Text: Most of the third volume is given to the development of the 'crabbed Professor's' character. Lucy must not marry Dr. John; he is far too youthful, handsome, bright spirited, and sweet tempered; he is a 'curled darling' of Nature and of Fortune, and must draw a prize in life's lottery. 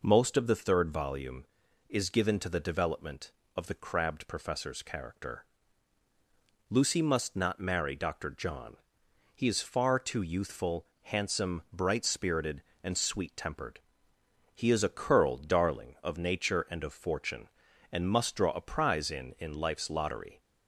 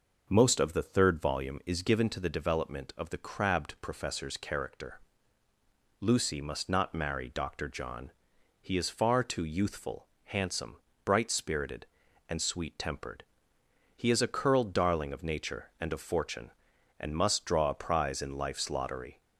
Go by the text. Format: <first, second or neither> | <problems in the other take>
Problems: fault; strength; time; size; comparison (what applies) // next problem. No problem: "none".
second | says "in" twice; at 19.3 s